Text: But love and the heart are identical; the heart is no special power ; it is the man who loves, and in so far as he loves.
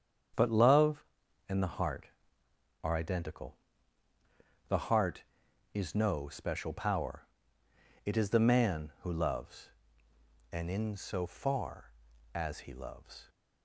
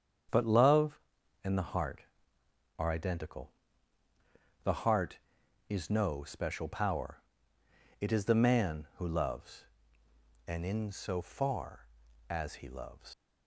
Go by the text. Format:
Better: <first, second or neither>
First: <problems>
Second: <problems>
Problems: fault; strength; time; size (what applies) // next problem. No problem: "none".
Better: first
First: starts louder than the rest; strong; until 1.8 s; 8 dB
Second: starts louder than the rest; strong; until 1.7 s; 8 dB // leaves "loves" unfinished; at 13.1 s; 105 ms